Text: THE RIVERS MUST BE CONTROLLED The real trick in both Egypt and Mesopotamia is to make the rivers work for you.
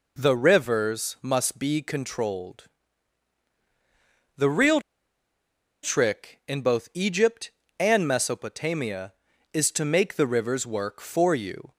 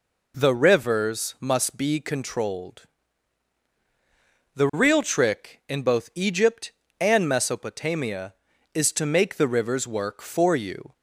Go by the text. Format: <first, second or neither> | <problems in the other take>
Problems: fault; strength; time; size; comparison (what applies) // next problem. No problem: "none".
second | pauses between "CONTROLLED" and "The"; strong; at 2.6 s; 1.7 s long; strong in the second // pauses between "real" and "trick"; at 4.8 s; 1.0 s long